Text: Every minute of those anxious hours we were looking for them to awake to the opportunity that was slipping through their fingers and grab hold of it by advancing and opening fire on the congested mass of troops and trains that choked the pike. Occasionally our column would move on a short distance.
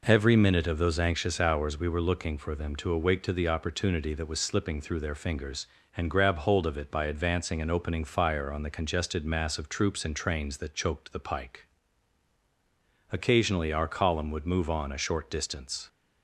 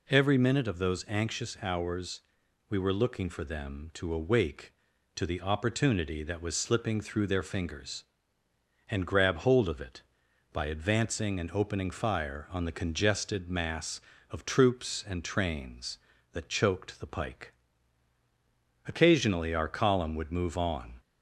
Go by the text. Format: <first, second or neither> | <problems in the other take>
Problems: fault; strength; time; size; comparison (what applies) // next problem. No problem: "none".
first | pauses between "hours" and "we"; noticeable; at 2.1 s; 0.50 s long // stops before "a short distance"; at 20.9 s